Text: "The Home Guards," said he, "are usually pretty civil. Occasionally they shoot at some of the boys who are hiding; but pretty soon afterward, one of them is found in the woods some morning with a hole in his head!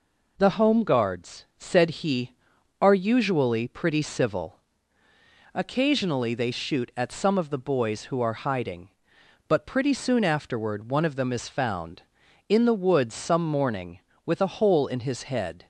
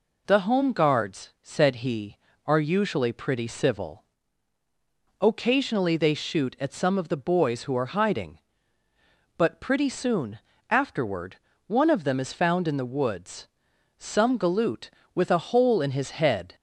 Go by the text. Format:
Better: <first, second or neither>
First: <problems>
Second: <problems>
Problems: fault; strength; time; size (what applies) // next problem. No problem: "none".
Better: first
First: none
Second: pauses between "soon" and "afterward"; slight; at 10.3 s; 0.32 s long // pauses between "woods" and "some"; noticeable; at 13.4 s; 0.52 s long // says "galoot" for "morning"; at 14.3 s